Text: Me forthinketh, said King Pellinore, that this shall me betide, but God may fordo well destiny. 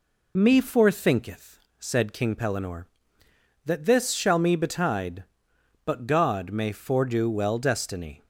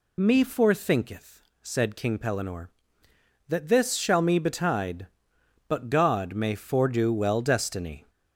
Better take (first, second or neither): first